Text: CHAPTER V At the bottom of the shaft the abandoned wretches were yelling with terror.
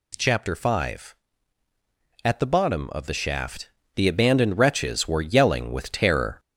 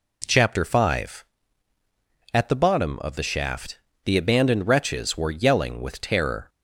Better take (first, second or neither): second